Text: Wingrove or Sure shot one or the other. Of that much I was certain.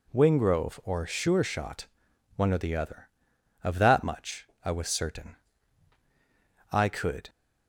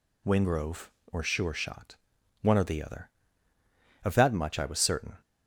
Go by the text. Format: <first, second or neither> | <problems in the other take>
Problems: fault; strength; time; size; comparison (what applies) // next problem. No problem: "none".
second | pauses between "shot" and "one"; noticeable; at 1.8 s; 0.48 s long; noticeable in the second // pauses between "much" and "I"; slight; at 4.4 s; 0.18 s long // goes on to say "I could"; from 6.7 s on; 0.58 s long